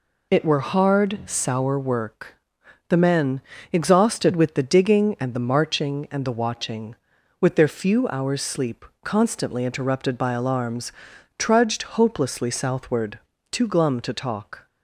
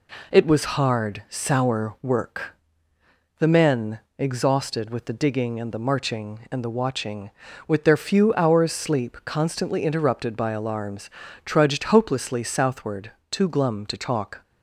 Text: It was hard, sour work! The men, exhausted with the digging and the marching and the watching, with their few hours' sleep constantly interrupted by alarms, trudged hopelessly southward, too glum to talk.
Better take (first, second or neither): second